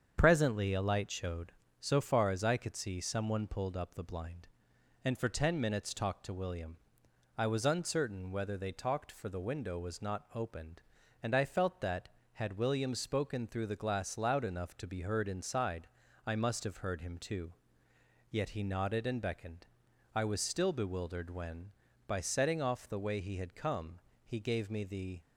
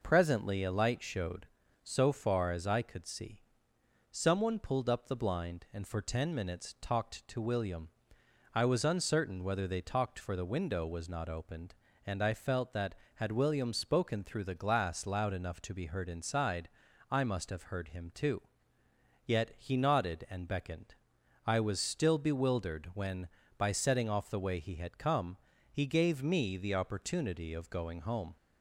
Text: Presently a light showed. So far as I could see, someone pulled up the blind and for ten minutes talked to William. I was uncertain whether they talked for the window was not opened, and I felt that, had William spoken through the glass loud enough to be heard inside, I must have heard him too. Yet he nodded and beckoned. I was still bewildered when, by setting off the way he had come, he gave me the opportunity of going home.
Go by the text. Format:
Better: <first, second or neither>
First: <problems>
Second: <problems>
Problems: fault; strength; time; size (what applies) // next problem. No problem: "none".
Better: second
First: starts louder than the rest; strong; until 1.2 s; 7.5 dB // stops before "opportunity of going home"; at 25.2 s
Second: none